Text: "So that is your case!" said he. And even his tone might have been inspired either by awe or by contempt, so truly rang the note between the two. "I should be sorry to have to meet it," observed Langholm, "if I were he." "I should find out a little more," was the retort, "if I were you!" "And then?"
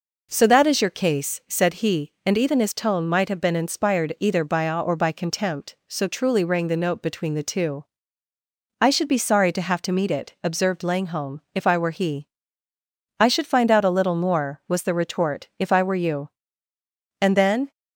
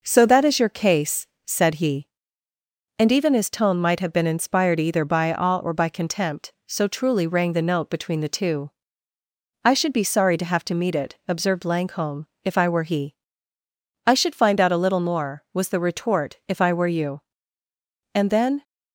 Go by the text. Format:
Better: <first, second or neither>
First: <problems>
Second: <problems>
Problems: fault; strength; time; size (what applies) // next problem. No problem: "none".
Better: neither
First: none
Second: none